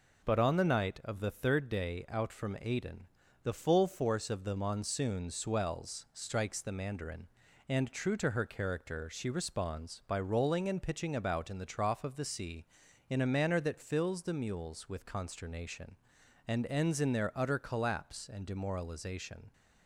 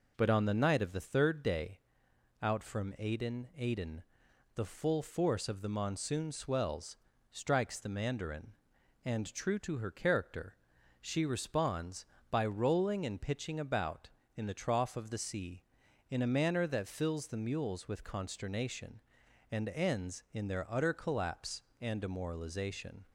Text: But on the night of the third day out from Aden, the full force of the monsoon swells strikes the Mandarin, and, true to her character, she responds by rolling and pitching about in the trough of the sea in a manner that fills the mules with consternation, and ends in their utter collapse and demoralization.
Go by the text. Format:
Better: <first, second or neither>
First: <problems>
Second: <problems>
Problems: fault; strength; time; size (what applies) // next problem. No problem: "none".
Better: first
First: none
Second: pauses between "day" and "out"; noticeable; at 1.7 s; 0.62 s long // says "Aden" twice; at 3.5 s // pauses between "swells" and "strikes"; slight; at 6.9 s; 0.34 s long